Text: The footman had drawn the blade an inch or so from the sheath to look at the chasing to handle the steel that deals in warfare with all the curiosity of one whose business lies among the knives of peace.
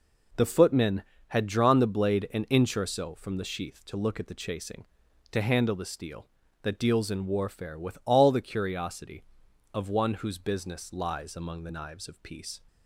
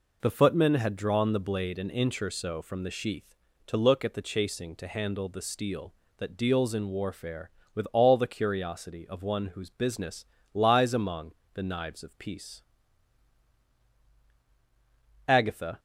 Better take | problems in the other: first | pauses between "business" and "lies"; slight; at 10.2 s; 0.28 s long // pauses between "among" and "the"; slight; at 11.3 s; 0.20 s long // goes on to say "Agatha"; from 15.2 s on; 0.52 s long

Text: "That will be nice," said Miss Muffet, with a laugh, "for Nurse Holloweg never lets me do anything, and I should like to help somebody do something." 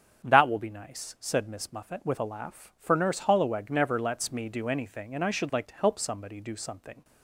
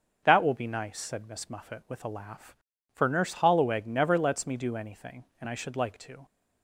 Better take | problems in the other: first | starts louder than the rest; until 1.2 s; 6.5 dB; strong in the first // stops before "help somebody do something"; at 6.2 s

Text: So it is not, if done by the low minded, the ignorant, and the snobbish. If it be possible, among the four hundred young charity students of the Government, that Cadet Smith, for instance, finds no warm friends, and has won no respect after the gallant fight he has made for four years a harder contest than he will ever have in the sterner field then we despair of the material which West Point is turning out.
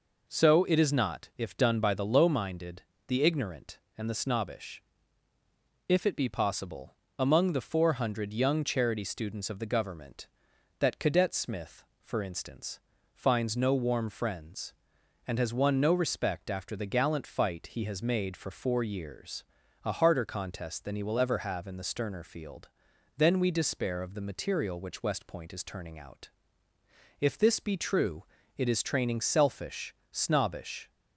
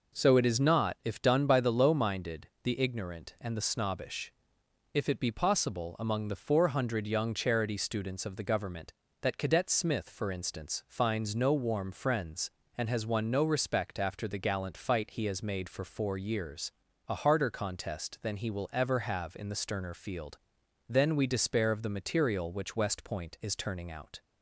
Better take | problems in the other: second | pauses between "years" and "a"; at 19.4 s; 0.42 s long; also in the second // pauses between "field" and "then"; noticeable; at 22.6 s; 0.48 s long; noticeable in the second // goes on to say "If this be true it is training selfish snobbish"; strong; from 27.1 s on; 3.7 s long

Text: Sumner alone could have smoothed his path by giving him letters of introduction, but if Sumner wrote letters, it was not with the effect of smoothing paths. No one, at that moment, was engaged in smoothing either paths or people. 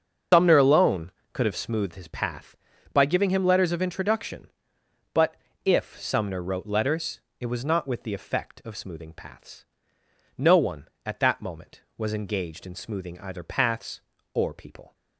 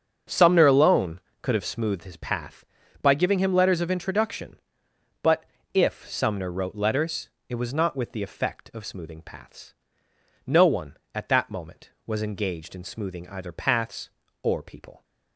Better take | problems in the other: second | loses the start of "Sumner"; at 0.3 s; 140 ms // starts louder than the rest; until 1.5 s; 7 dB; also in the second // pauses between "but" and "if"; slight; at 5.3 s; 0.28 s long; slight in the second

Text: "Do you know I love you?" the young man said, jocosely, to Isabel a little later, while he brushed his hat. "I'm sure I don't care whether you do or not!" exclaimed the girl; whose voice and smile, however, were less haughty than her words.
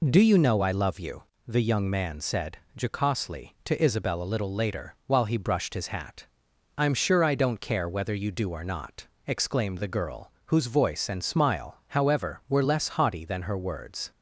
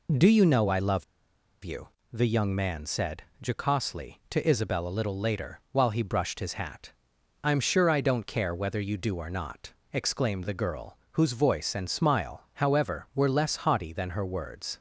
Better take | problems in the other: first | pauses between "love" and "you"; noticeable; at 1.0 s; 0.60 s long

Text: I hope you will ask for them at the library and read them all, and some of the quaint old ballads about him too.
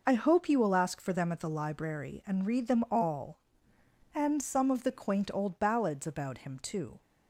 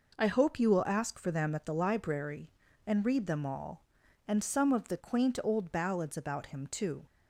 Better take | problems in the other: neither | none

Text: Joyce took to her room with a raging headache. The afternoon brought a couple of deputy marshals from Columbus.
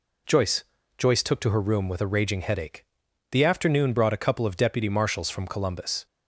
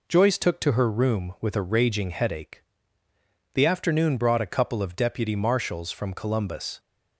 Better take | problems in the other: second | says "Joyce" twice; at 0.9 s

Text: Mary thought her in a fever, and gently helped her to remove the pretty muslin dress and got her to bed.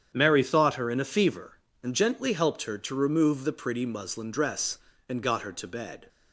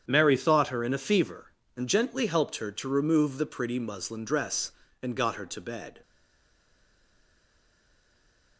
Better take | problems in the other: first | starts louder than the rest; strong; until 1.0 s; 8.5 dB; strong in the first // stays silent after the last word; strong; from 6.0 s on; 2.5 s long

